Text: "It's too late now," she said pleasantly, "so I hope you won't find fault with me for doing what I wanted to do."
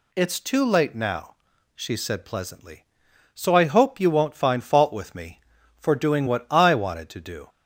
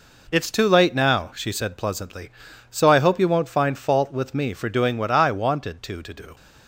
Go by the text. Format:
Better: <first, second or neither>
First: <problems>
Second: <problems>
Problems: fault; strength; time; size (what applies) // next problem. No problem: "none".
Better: first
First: none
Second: says "to" twice; at 6.0 s